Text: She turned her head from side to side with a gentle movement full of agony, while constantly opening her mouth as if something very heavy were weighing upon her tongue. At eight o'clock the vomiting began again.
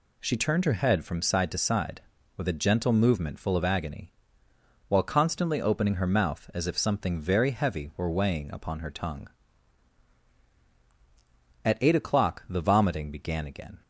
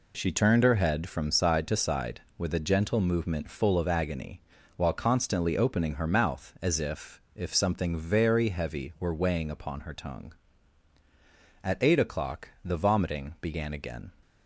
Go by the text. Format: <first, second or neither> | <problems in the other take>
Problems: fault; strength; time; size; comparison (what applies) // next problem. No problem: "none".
first | says "if" twice; at 7.3 s // pauses between "o'clock" and "the"; slight; at 12.4 s; 0.16 s long